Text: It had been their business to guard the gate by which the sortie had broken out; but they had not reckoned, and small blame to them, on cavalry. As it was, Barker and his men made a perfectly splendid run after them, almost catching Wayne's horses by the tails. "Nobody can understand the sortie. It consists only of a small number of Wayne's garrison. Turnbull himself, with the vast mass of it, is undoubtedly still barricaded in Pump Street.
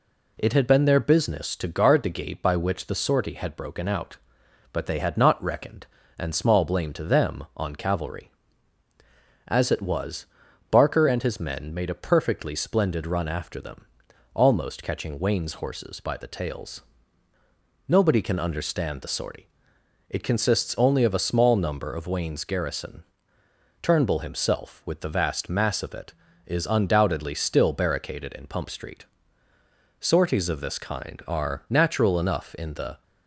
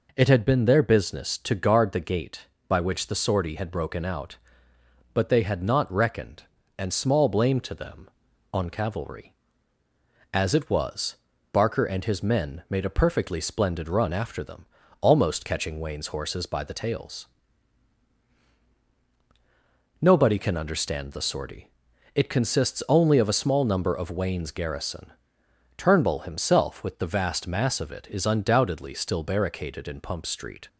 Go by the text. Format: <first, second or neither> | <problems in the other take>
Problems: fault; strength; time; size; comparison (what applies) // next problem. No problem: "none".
second | goes on to say "Sorties of this kind are natural enough in the"; strong; from 29.9 s on; 3.0 s long